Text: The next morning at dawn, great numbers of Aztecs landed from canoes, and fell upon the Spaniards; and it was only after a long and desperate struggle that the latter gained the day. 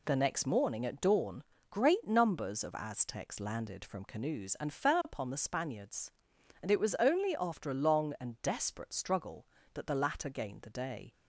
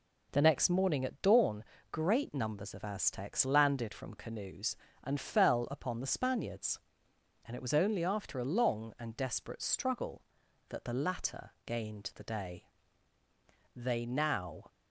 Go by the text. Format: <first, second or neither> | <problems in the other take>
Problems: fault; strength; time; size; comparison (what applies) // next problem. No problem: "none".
first | goes on to say "They now"; noticeable; from 13.7 s on; 0.90 s long